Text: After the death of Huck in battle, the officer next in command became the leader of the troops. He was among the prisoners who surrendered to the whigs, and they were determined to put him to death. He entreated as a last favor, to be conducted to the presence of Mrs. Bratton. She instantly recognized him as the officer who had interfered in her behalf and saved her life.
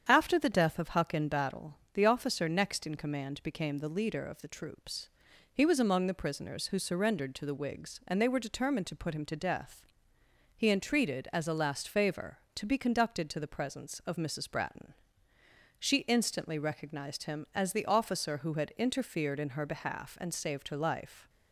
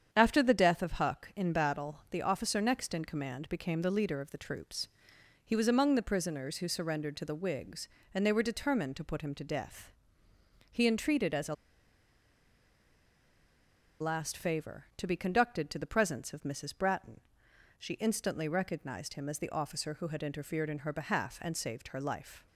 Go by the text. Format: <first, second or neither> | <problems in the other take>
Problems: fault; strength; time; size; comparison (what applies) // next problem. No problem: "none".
first | starts louder than the rest; strong; until 1.1 s; 8.5 dB; strong in the first // pauses between "a" and "last"; strong; at 11.5 s; 2.4 s long